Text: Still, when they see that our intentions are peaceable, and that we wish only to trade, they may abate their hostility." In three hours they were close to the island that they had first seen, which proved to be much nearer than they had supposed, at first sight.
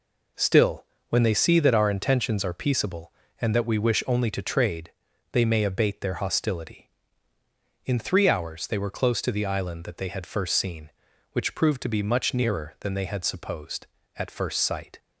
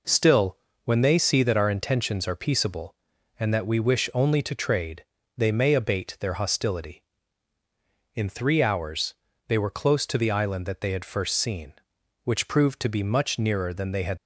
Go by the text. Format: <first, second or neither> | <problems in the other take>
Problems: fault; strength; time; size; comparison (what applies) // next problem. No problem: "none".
first | pauses between "hours" and "they"; slight; at 9.1 s; 0.34 s long // stops before "supposed at first sight"; at 14.1 s